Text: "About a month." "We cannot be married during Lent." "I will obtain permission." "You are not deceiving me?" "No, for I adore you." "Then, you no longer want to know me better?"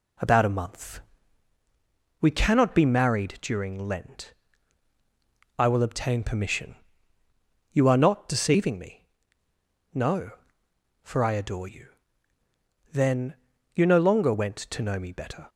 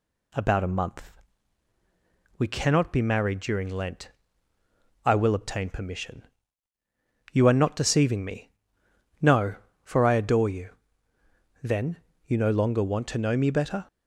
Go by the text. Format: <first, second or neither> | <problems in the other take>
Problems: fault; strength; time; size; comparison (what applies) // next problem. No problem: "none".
second | says "went" for "want"; at 14.3 s